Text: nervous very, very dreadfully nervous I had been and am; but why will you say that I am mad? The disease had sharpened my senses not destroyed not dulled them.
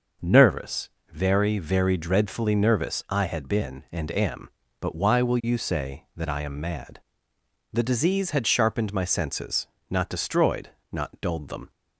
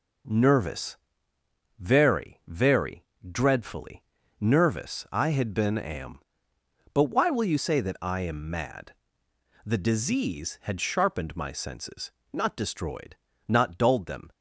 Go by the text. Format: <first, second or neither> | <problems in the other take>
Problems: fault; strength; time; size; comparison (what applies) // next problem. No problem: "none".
first | pauses between "nervous" and "very"; noticeable; at 0.9 s; 0.82 s long; slight in the first // pauses between "very" and "dreadfully"; slight; at 3.0 s; 0.26 s long // pauses between "dreadfully" and "nervous"; at 4.0 s; 0.38 s long // skips "and"; at 5.7 s // pauses between "senses" and "not"; slight; at 12.1 s; 0.22 s long; slight in the first // pauses between "destroyed" and "not"; slight; at 13.1 s; 0.30 s long; slight in the first